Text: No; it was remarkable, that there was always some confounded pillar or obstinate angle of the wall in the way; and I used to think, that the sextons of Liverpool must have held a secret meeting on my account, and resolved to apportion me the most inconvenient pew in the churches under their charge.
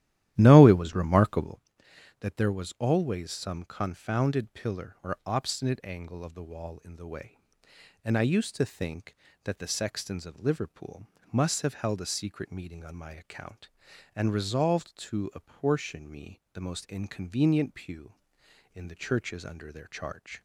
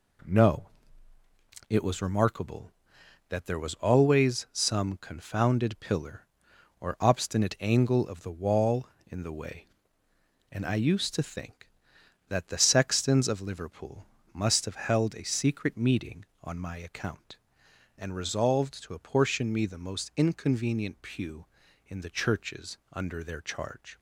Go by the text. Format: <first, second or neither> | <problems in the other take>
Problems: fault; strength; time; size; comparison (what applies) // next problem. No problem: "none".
second | starts louder than the rest; strong; until 1.6 s; 13 dB // pauses between "Liverpool" and "must"; slight; at 11.0 s; 0.24 s long; slight in the second